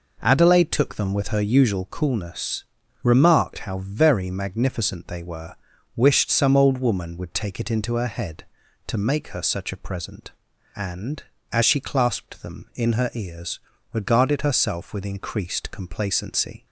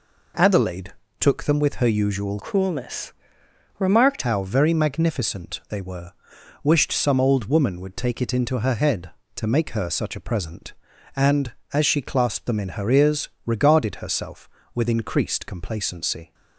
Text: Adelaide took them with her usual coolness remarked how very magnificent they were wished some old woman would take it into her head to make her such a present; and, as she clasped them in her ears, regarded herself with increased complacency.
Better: first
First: pauses between "coolness" and "remarked"; at 2.6 s; 0.40 s long // pauses between "were" and "wished"; at 5.5 s; 0.40 s long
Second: pauses between "Adelaide" and "took"; slight; at 0.9 s; 0.30 s long // changes voice from "coolness" to "remarked"; from 2.4 to 4.2 s; 1.8 s long // pauses between "coolness" and "remarked"; noticeable; at 3.1 s; 0.66 s long // pauses between "were" and "wished"; noticeable; at 6.1 s; 0.52 s long

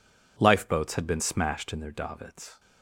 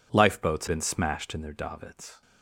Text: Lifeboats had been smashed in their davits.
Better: first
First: none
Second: skips "had"; at 0.6 s

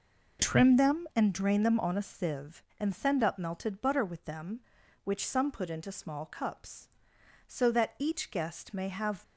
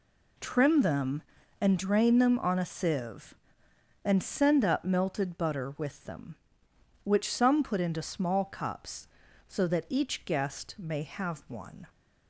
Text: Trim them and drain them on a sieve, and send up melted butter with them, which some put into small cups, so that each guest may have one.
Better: second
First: stops before "one"; at 9.2 s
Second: none

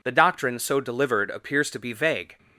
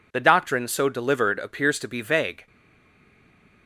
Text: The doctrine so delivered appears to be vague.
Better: first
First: none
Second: stays silent after the last word; noticeable; from 2.4 s on; 1.2 s long

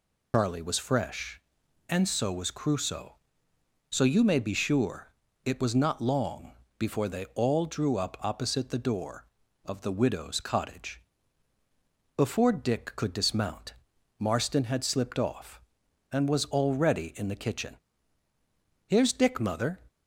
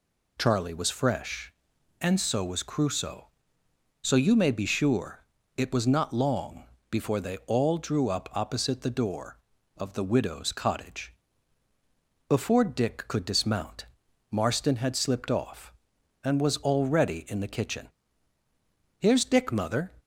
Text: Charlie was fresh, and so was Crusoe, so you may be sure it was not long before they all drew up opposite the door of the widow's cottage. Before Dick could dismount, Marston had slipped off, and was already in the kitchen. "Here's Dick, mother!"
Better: second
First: loses the start of "Charlie"; at 0.3 s; 75 ms // pauses between "sure" and "it"; slight; at 5.1 s; 0.32 s long // pauses between "long" and "before"; slight; at 6.5 s; 0.26 s long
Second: pauses between "sure" and "it"; slight; at 5.2 s; 0.32 s long // pauses between "long" and "before"; slight; at 6.6 s; 0.26 s long

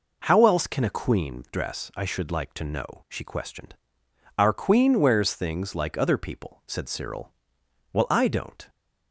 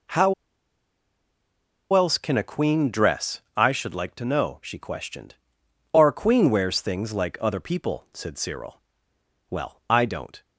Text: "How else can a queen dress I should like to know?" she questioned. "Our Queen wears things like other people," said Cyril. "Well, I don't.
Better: first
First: none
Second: pauses between "How" and "else"; strong; at 0.3 s; 1.6 s long // pauses between "dress" and "I"; slight; at 3.3 s; 0.16 s long

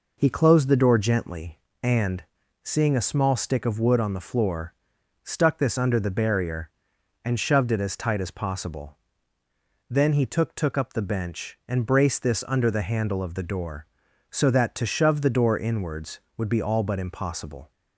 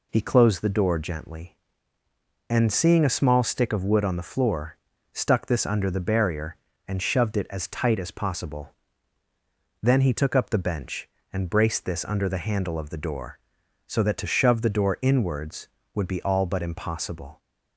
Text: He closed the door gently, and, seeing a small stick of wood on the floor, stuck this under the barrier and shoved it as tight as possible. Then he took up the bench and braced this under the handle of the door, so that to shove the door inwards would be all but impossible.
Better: second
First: says "took" twice; at 10.5 s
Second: none

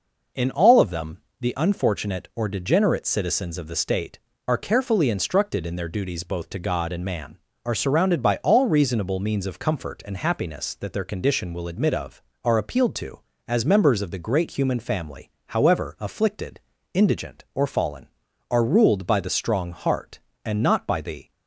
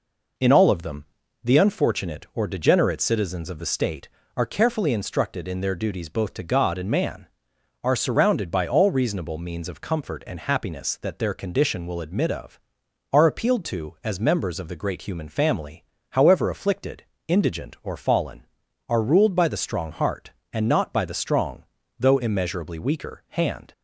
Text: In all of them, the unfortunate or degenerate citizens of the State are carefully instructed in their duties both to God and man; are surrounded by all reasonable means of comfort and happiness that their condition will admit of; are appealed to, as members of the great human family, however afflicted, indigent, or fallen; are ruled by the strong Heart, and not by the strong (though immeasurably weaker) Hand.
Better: second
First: stops before "strong though immeasurably weaker Hand"; at 21.3 s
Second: none

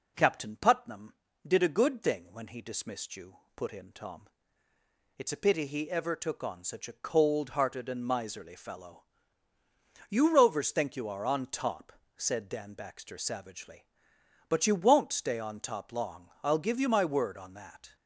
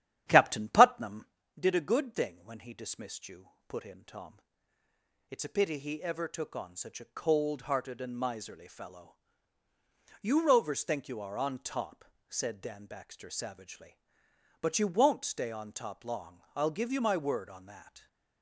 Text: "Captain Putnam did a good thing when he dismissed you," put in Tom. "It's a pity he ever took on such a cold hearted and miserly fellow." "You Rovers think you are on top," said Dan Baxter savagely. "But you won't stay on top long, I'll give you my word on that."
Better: first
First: none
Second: starts louder than the rest; strong; until 1.5 s; 11 dB

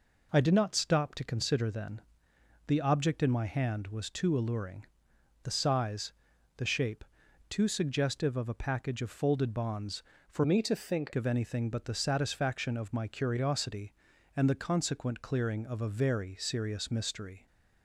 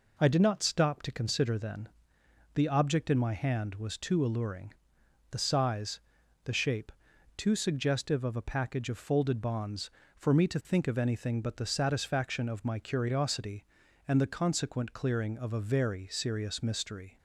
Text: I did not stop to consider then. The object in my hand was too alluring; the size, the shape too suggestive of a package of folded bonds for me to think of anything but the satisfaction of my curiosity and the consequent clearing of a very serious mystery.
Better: second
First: pauses between "shape" and "too"; noticeable; at 7.0 s; 0.46 s long // changes voice from "me" to "think"; from 10.4 to 11.1 s; 0.7 s long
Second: pauses between "shape" and "too"; noticeable; at 6.9 s; 0.46 s long

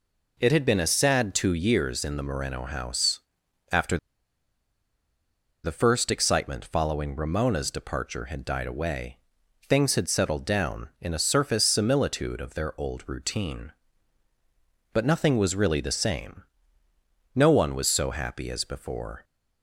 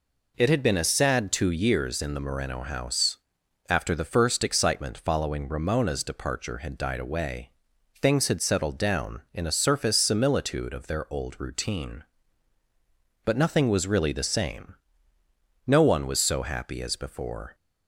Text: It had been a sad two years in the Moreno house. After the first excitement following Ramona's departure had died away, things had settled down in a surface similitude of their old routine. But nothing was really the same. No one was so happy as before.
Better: second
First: pauses between "After" and "the"; strong; at 3.9 s; 1.6 s long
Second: none

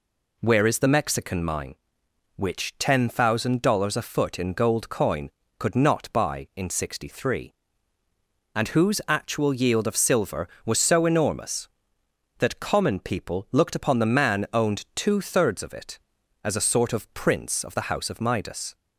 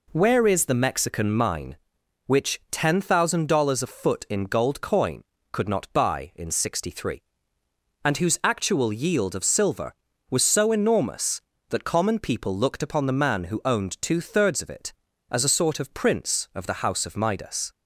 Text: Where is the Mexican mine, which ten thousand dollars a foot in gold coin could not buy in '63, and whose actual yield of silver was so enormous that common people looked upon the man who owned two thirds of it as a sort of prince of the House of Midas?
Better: second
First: skips "who"; at 14.4 s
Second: none

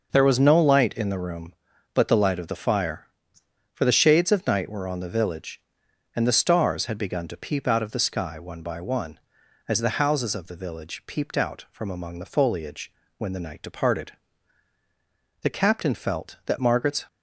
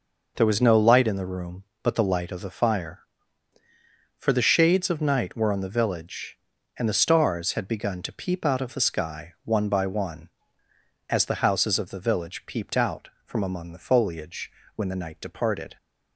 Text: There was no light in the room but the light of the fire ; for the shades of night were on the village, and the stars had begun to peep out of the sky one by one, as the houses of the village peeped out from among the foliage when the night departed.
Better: second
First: pauses between "foliage" and "when"; slight; at 12.9 s; 0.26 s long // goes on to say "The captain felt that Margaret's"; from 15.4 s on; 1.6 s long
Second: pauses between "foliage" and "when"; slight; at 14.5 s; 0.24 s long

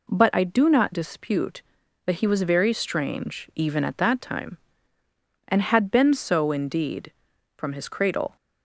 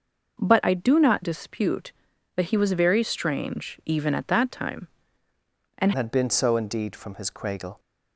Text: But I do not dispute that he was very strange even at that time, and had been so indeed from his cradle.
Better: first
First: none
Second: changes voice at "had"; from 5.9 s on; 1.8 s long

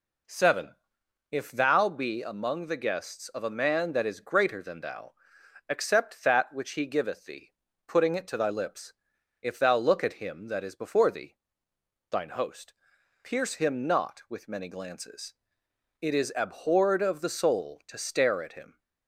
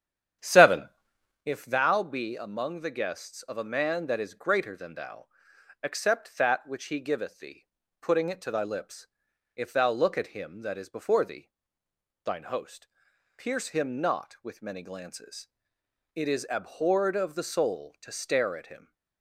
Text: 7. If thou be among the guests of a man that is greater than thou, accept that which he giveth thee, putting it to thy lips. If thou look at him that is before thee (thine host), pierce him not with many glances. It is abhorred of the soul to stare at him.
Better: first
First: none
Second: starts louder than the rest; strong; until 1.5 s; 9.5 dB

